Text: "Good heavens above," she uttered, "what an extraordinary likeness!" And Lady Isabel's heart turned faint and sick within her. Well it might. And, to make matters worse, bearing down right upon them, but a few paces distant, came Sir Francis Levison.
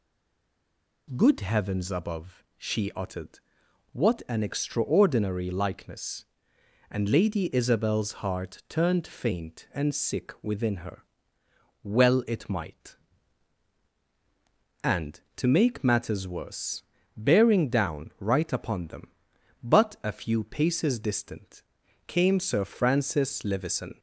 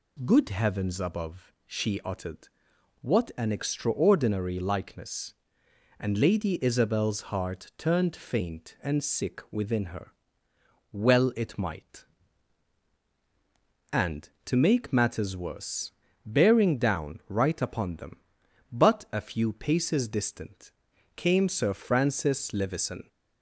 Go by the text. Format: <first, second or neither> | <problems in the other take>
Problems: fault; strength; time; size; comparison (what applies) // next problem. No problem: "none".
second | stays silent before the first word; until 1.0 s; 1.0 s long